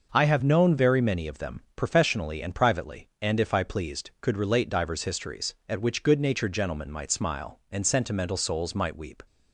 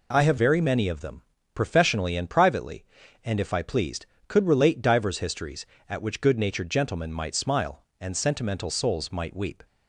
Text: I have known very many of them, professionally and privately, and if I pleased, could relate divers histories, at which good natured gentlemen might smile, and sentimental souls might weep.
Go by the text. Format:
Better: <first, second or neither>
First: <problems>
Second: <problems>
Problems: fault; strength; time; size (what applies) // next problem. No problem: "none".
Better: first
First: none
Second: skips "known"; at 0.3 s